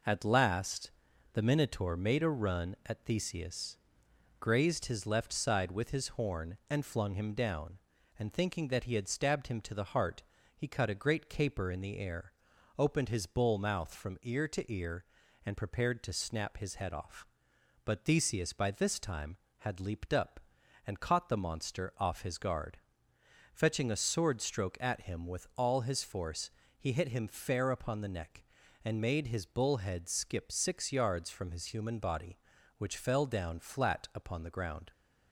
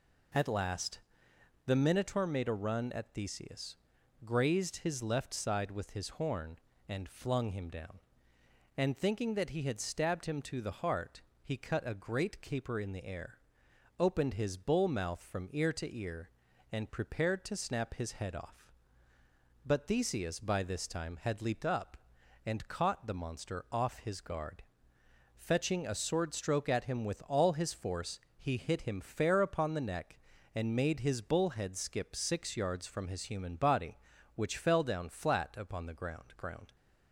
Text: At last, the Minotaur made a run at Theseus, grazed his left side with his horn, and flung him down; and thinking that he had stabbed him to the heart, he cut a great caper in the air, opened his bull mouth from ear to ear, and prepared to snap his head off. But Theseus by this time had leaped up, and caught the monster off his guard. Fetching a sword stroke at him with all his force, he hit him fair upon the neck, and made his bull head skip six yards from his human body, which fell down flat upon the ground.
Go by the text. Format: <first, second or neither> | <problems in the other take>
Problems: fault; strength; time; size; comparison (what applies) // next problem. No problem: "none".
first | says "ground" twice; at 36.3 s